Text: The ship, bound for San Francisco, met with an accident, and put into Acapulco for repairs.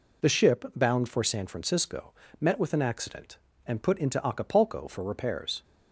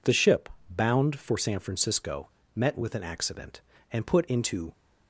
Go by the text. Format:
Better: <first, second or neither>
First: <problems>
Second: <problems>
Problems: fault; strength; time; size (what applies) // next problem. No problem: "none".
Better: first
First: none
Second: stops before "Acapulco for repairs"; at 4.7 s